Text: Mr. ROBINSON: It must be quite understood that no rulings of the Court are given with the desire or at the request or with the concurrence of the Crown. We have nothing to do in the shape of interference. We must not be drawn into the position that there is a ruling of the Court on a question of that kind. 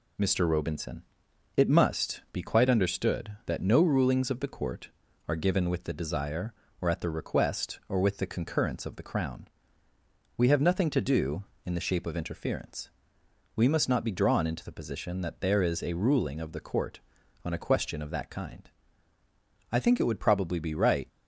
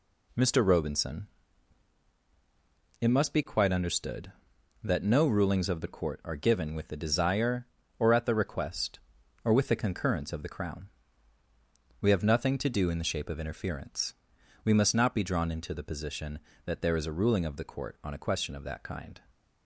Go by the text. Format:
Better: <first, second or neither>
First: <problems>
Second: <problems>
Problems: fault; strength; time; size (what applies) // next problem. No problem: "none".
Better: second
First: goes on to say "I think it would probably be right"; from 19.6 s on; 1.3 s long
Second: none